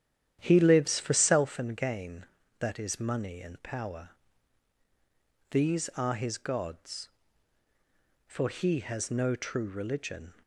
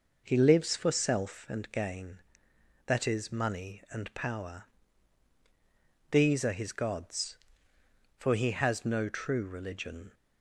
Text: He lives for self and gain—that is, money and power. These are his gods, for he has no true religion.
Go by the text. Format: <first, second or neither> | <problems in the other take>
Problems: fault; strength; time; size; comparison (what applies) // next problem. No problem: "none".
second | starts louder than the rest; strong; until 1.5 s; 10 dB